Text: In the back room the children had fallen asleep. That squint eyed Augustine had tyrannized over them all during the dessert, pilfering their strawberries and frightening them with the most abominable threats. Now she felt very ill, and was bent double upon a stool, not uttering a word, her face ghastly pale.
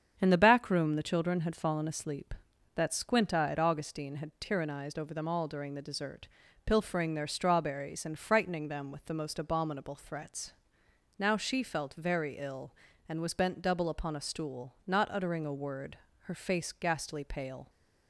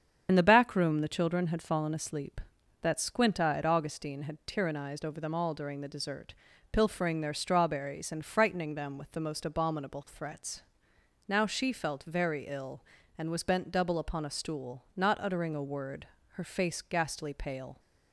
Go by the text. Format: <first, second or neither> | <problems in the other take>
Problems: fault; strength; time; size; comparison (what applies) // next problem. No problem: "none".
first | loses the start of "In"; at 0.2 s; 55 ms // starts louder than the rest; strong; until 1.3 s; 8 dB; strong in the first